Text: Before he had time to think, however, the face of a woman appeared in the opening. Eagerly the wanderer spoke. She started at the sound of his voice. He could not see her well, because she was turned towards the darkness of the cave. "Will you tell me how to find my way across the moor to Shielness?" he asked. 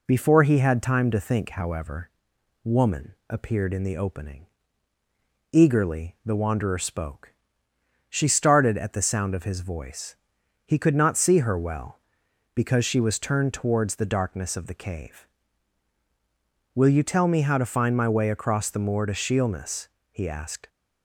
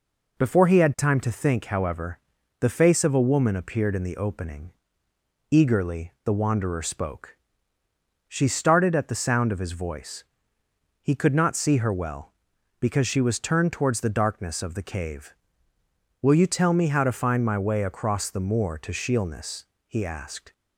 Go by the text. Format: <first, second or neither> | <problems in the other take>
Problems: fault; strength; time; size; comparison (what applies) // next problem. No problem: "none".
second | skips "the face of a"; at 2.3 s